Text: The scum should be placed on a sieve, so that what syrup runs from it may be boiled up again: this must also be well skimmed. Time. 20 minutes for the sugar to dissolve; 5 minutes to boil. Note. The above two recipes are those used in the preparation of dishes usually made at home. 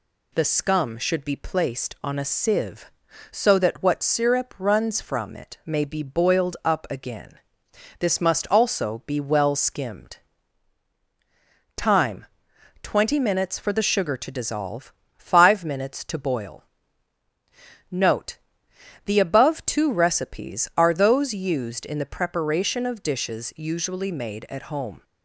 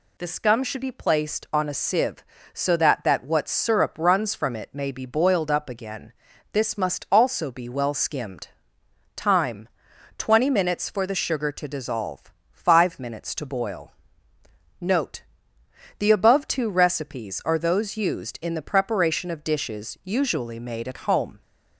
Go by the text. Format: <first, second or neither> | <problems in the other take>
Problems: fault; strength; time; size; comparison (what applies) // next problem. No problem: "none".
first | says "that" twice; at 3.0 s